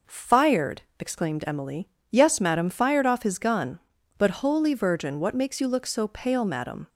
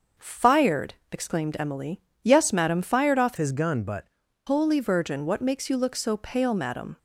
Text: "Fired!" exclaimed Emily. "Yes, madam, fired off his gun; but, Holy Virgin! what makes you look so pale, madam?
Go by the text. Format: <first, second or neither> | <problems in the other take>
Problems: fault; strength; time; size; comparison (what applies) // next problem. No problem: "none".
first | starts louder than the rest; noticeable; until 1.3 s; 6 dB // changes voice from "his" to "but"; from 3.3 to 4.0 s; 0.7 s long